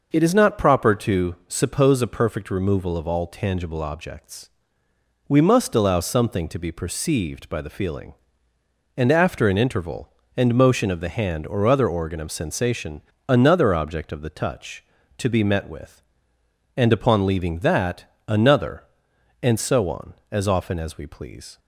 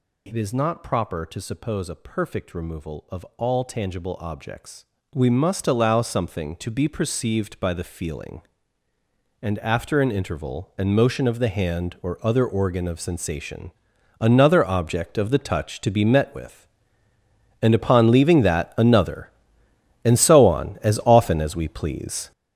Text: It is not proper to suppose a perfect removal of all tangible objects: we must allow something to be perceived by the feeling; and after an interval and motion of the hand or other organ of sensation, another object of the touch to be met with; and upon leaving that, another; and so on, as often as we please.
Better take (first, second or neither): first